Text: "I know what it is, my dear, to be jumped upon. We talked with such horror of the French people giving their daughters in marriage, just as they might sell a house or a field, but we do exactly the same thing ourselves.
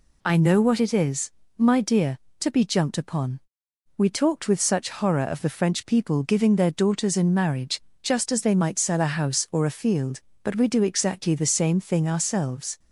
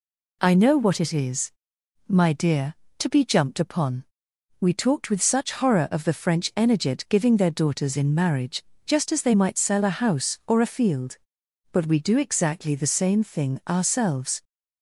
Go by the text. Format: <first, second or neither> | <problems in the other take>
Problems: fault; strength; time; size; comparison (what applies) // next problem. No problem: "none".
first | says "energet" for "people"; at 6.5 s